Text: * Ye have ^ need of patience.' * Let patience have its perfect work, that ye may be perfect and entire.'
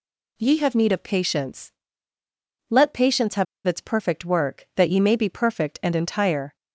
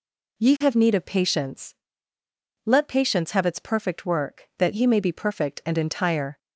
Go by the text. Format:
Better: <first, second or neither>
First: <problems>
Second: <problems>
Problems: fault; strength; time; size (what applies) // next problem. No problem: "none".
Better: second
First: pauses between "have" and "its"; slight; at 3.4 s; 0.22 s long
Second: none